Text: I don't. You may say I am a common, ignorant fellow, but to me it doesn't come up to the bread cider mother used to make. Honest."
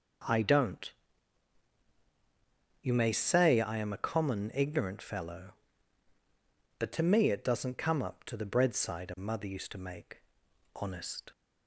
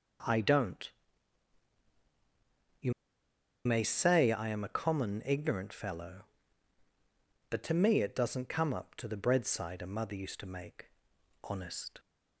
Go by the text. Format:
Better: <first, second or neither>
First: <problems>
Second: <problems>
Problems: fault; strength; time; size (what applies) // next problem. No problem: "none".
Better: first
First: none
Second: pauses between "You" and "may"; noticeable; at 2.9 s; 0.74 s long